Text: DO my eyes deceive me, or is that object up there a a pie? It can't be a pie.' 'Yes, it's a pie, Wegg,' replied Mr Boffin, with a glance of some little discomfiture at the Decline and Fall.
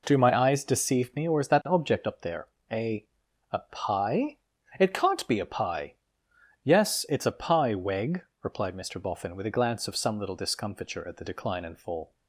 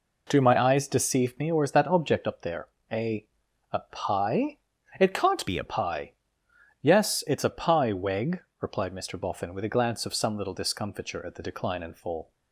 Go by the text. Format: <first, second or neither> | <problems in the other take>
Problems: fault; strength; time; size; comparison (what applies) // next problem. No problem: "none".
first | pauses between "there" and "a"; slight; at 2.6 s; 0.24 s long; slight in the first // pauses between "a" and "a"; noticeable; at 3.2 s; 0.46 s long; noticeable in the first // changes voice from "be" to "a"; from 5.4 to 5.6 s; 0.2 s long